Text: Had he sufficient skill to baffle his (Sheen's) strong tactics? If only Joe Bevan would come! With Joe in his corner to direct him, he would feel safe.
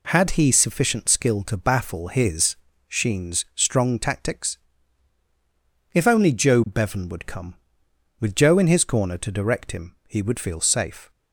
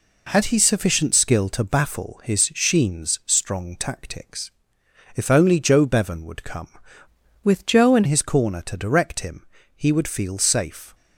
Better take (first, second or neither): first